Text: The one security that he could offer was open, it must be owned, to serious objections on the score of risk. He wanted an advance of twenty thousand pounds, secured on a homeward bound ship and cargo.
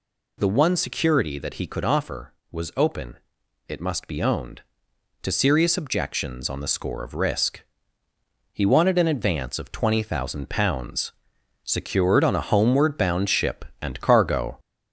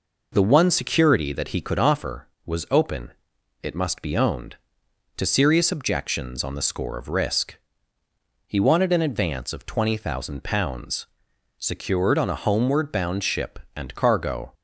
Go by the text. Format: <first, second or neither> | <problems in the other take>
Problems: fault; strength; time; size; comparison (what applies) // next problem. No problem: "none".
second | gets louder; throughout; 3.5 dB